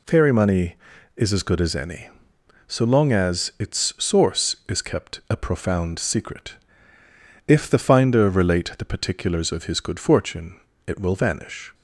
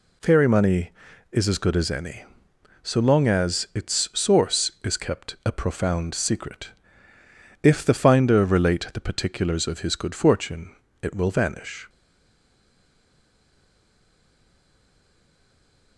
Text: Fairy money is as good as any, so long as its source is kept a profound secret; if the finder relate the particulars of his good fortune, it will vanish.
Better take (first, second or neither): first